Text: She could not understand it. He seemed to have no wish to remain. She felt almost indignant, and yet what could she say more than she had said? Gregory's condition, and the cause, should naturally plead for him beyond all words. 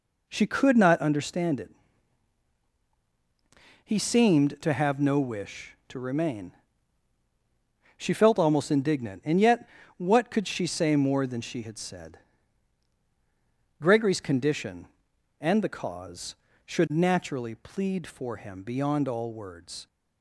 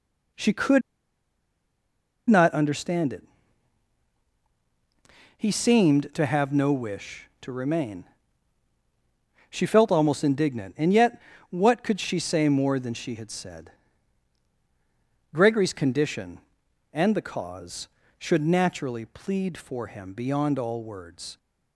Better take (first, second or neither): first